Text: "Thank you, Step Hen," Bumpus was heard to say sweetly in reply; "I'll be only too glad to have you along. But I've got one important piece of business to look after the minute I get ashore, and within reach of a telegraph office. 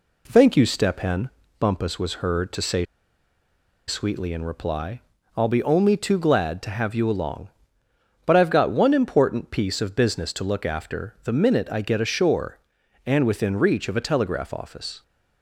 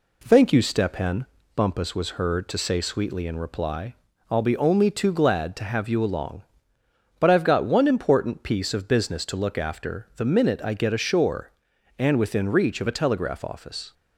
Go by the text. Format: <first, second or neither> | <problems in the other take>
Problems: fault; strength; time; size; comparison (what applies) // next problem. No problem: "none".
second | pauses between "say" and "sweetly"; at 2.8 s; 1.0 s long